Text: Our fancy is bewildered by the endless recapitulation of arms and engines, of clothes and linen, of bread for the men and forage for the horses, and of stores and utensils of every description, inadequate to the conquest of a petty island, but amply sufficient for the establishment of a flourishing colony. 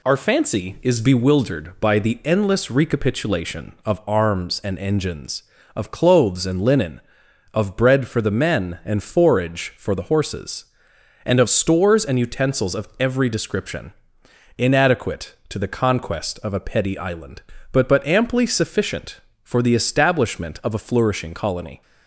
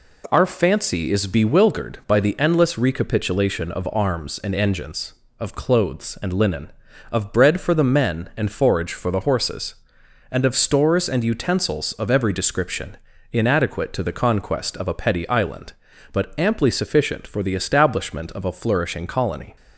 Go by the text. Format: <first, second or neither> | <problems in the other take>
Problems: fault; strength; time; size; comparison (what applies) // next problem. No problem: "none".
second | says "but" twice; at 17.8 s